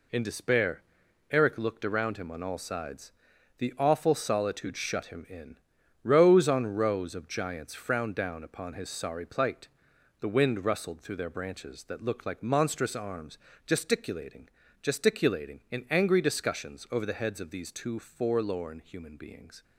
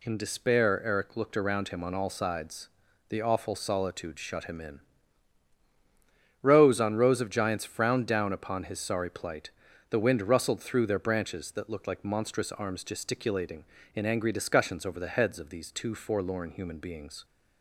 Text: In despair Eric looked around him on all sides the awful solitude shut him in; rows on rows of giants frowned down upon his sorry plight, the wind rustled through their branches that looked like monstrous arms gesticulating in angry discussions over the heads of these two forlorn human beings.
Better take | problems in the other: second | pauses between "despair" and "Eric"; noticeable; at 0.8 s; 0.48 s long // pauses between "sides" and "the"; noticeable; at 3.1 s; 0.48 s long; also in the second // pauses between "arms" and "gesticulating"; slight; at 13.3 s; 0.30 s long // says "gesticulating" twice; at 14.8 s

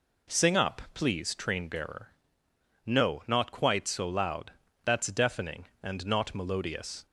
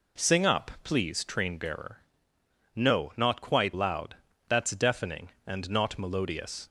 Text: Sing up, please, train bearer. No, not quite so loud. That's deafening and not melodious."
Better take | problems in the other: first | skips "so"; at 3.7 s

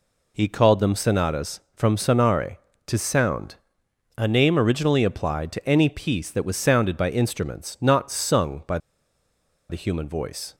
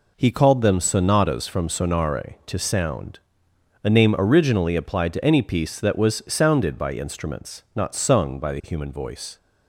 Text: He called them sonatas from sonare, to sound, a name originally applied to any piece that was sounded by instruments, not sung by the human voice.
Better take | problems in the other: second | pauses between "by" and "the"; noticeable; at 8.7 s; 0.92 s long

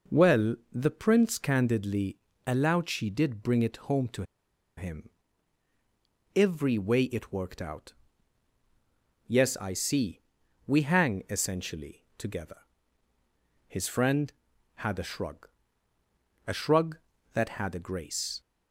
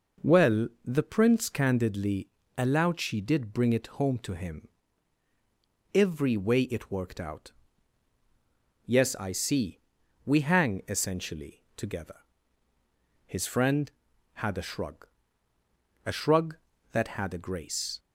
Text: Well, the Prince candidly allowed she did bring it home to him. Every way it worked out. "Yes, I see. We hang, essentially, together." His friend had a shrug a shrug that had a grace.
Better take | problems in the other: second | pauses between "candidly" and "allowed"; slight; at 2.1 s; 0.28 s long; slight in the second // pauses between "to" and "him"; noticeable; at 4.2 s; 0.54 s long // pauses between "shrug" and "a"; noticeable; at 15.4 s; 0.98 s long; noticeable in the second

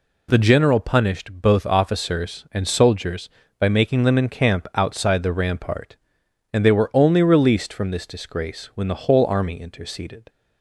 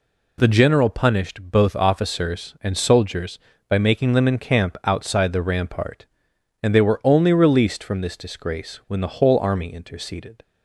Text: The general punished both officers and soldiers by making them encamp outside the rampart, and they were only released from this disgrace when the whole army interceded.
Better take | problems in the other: neither | none

